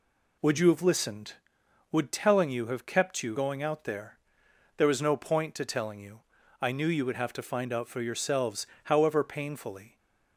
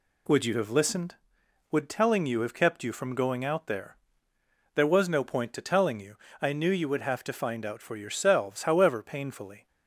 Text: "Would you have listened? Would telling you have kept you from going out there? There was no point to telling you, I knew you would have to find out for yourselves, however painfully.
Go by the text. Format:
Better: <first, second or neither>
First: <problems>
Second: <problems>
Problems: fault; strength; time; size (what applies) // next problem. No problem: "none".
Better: second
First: skips "from"; at 3.3 s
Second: none